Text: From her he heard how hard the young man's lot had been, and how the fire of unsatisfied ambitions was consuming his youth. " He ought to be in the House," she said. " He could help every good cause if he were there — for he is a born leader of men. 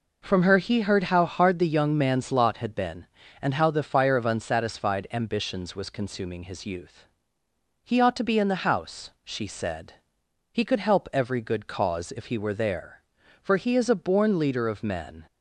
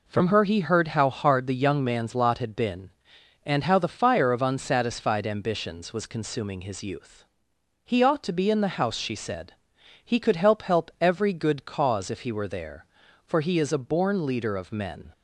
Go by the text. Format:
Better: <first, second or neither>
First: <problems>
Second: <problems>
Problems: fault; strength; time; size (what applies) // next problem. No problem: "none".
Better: first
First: none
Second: says "help" twice; at 10.6 s